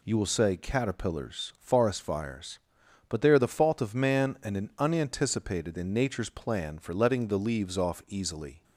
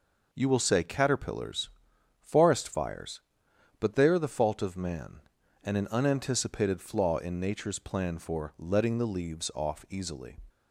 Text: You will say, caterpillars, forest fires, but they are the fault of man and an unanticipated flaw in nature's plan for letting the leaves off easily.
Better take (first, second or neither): second